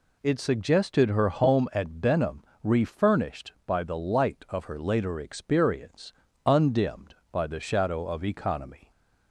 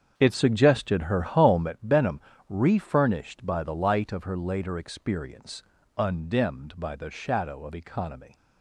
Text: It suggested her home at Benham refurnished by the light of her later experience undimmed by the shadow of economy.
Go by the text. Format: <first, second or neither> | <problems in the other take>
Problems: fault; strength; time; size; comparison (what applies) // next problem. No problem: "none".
first | starts louder than the rest; strong; until 1.7 s; 7.5 dB // pauses between "Benham" and "refurnished"; slight; at 2.2 s; 0.26 s long; slight in the first // pauses between "experience" and "undimmed"; slight; at 5.6 s; 0.36 s long; slight in the first